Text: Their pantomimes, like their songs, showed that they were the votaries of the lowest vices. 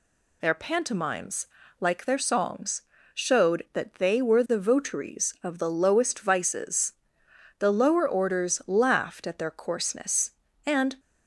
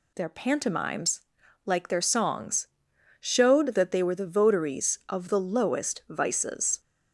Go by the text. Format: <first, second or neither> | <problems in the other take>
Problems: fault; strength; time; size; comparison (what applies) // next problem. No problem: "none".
second | goes on to say "The lower orders laughed at their coarseness and"; strong; from 7.5 s on; 3.3 s long